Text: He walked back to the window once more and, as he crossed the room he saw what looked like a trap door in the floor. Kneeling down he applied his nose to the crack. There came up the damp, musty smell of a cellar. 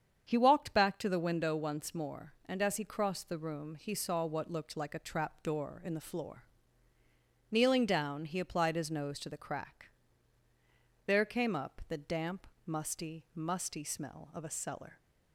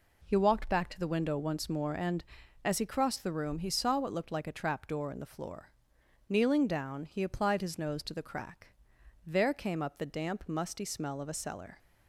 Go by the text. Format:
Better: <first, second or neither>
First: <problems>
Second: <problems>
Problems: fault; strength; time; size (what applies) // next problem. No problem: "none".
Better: second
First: starts louder than the rest; strong; until 1.2 s; 7.5 dB // says "musty" twice; at 13.3 s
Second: none